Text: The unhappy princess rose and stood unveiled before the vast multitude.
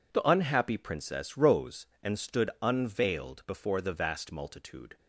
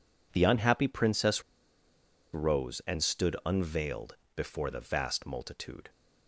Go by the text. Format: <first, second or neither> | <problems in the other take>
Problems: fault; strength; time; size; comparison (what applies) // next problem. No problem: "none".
first | pauses between "princess" and "rose"; noticeable; at 1.4 s; 0.90 s long // pauses between "unveiled" and "before"; slight; at 4.1 s; 0.20 s long